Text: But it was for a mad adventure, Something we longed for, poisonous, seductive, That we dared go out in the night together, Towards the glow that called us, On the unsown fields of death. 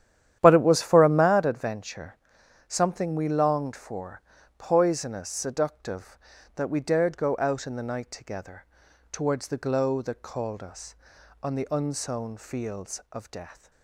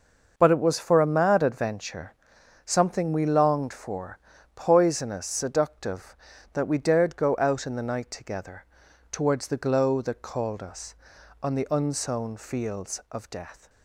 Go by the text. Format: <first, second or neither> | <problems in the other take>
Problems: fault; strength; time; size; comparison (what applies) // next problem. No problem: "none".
second | starts louder than the rest; strong; until 1.4 s; 10.5 dB